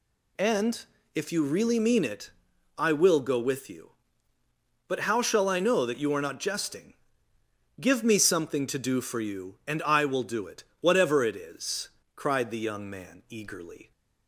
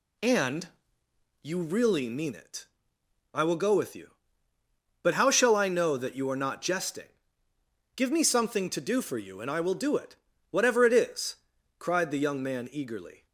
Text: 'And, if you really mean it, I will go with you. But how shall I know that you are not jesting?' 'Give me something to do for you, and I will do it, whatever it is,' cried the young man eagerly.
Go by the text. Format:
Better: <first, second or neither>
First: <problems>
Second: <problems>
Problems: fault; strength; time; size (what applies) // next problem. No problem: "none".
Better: first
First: none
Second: skips "if"; at 1.0 s